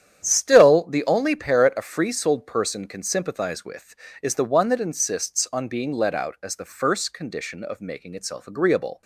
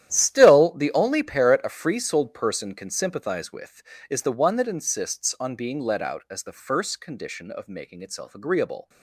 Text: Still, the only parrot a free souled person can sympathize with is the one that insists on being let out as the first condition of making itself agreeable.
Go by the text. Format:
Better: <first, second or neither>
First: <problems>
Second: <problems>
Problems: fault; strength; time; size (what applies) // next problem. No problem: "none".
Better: first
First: starts louder than the rest; strong; until 1.2 s; 9.5 dB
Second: gets quieter; strong; throughout; 14.5 dB // starts louder than the rest; strong; until 1.1 s; 11.5 dB